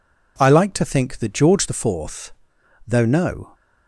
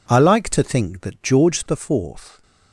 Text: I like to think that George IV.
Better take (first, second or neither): second